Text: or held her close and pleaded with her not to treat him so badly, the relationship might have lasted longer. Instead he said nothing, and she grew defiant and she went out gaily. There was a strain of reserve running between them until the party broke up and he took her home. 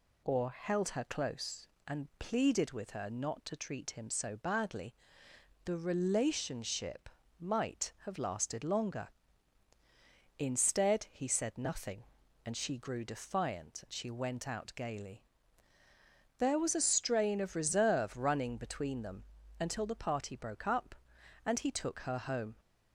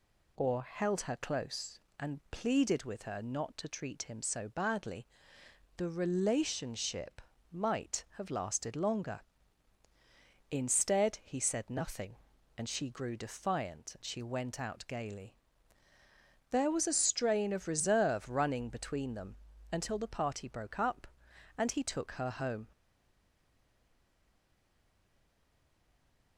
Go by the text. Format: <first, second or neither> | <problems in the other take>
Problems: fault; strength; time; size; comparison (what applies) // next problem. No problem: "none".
first | pauses between "relationship" and "might"; slight; at 7.2 s; 0.30 s long; slight in the first // pauses between "them" and "until"; slight; at 19.3 s; 0.36 s long; slight in the first // stays silent after the last word; strong; from 22.7 s on; 3.6 s long